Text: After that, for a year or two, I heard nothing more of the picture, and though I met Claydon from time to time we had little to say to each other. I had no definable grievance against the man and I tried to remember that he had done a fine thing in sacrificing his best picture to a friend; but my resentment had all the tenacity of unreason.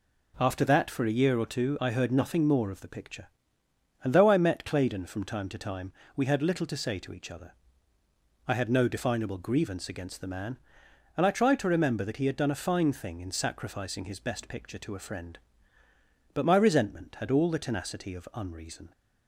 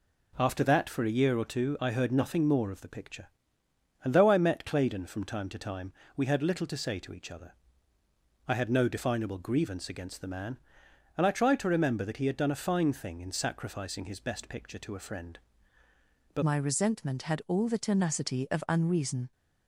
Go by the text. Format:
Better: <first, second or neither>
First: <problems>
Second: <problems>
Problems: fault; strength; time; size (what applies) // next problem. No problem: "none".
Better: first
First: pauses between "time" and "we"; slight; at 5.9 s; 0.24 s long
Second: pauses between "time" and "we"; slight; at 5.9 s; 0.24 s long // changes voice at "my"; from 16.4 s on; 2.9 s long